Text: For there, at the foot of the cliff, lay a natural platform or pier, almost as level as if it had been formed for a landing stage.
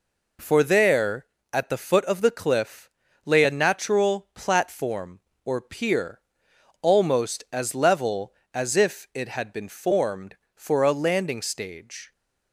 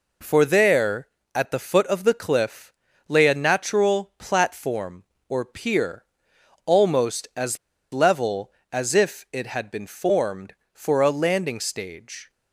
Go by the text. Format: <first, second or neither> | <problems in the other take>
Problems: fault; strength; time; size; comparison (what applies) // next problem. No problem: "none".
first | pauses between "as" and "level"; slight; at 7.5 s; 0.34 s long